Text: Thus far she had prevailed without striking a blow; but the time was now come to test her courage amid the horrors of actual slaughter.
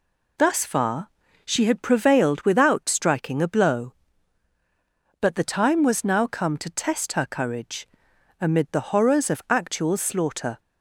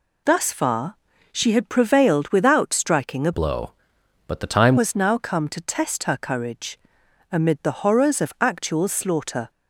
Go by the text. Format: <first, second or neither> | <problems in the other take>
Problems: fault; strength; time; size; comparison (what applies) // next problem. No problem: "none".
first | pauses between "far" and "she"; slight; at 0.9 s; 0.36 s long; slight in the first // changes voice from "blow" to "time"; from 3.3 to 4.7 s; 1.4 s long // pauses between "courage" and "amid"; noticeable; at 6.7 s; 0.54 s long; noticeable in the first